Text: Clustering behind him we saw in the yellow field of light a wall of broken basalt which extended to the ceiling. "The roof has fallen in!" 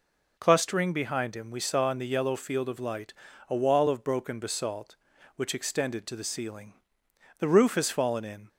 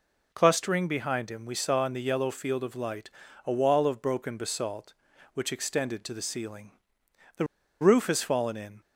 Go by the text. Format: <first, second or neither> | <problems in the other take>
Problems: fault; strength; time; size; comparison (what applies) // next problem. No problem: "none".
first | pauses between "light" and "a"; slight; at 3.0 s; 0.36 s long; slight in the first // pauses between "The" and "roof"; at 7.4 s; 0.37 s long